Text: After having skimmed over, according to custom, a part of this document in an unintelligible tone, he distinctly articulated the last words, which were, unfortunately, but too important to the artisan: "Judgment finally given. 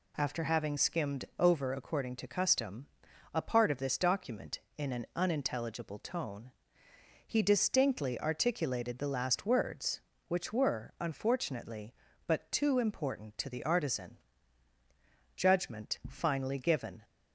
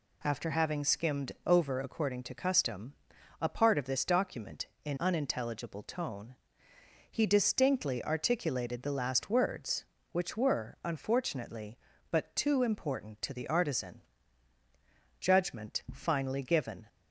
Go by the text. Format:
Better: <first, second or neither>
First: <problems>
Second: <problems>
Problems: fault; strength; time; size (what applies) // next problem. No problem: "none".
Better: first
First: none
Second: skips "an"; at 4.9 s